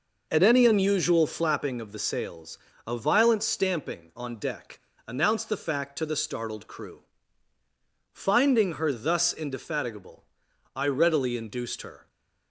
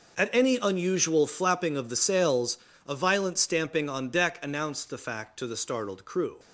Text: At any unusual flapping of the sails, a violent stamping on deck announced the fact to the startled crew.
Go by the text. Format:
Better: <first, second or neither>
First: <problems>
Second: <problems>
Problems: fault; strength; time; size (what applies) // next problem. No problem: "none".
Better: second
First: pauses between "deck" and "announced"; slight; at 4.7 s; 0.28 s long // goes on to say "Finding her thus indefatigable I readily induced her"; strong; from 8.1 s on; 3.9 s long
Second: none